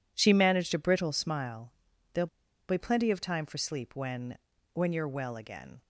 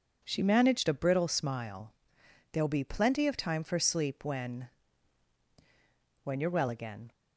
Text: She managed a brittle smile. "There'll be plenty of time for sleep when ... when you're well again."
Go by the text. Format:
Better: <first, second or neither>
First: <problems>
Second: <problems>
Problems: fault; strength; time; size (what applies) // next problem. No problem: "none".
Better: second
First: pauses between "There'll" and "be"; at 2.2 s; 0.41 s long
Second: none